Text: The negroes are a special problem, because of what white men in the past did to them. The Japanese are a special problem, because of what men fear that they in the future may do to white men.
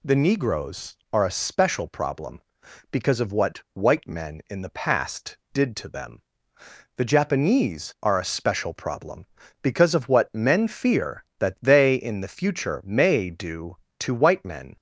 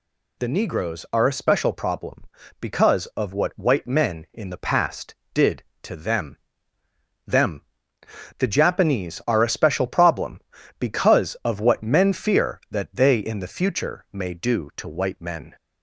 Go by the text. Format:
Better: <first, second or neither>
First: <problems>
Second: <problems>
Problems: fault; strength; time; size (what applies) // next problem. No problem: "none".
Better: first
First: none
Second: says "them" twice; at 7.2 s